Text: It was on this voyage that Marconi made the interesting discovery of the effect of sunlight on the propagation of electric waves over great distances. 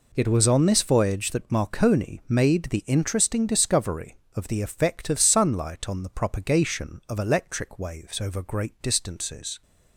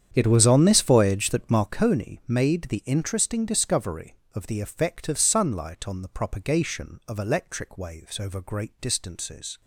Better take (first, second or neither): first